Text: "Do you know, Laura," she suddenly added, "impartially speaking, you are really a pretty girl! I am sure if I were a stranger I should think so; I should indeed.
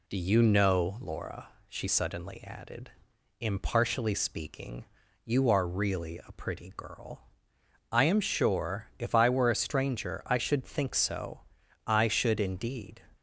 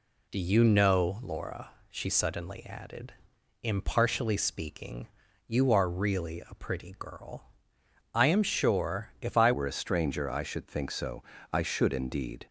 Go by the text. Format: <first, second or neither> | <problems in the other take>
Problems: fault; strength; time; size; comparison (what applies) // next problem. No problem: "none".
first | changes voice at "were"; from 9.5 s on; 2.9 s long